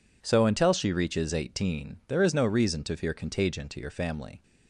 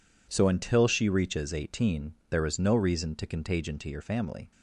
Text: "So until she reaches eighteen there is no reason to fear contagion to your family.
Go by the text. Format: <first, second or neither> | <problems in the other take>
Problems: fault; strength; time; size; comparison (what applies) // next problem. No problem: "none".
first | pauses between "eighteen" and "there"; slight; at 2.1 s; 0.16 s long // skips "fear"; at 3.2 s